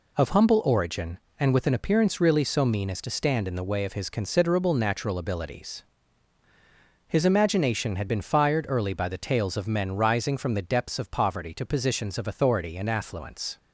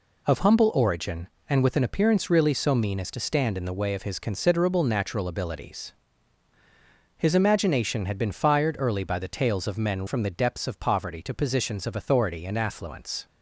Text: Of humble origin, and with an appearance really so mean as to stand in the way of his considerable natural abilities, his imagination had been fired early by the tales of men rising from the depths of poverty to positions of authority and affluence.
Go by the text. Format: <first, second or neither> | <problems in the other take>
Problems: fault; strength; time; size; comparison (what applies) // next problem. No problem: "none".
first | skips "rising"; at 10.0 s